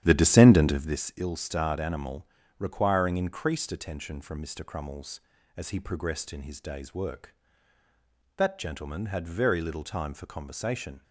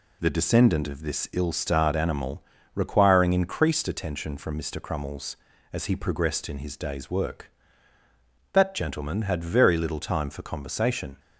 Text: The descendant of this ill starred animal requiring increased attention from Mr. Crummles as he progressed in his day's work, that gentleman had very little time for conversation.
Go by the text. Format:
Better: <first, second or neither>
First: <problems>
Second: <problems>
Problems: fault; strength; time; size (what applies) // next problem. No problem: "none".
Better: second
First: starts louder than the rest; strong; until 1.1 s; 10.5 dB // pauses between "animal" and "requiring"; slight; at 2.2 s; 0.32 s long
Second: pauses between "animal" and "requiring"; slight; at 2.4 s; 0.32 s long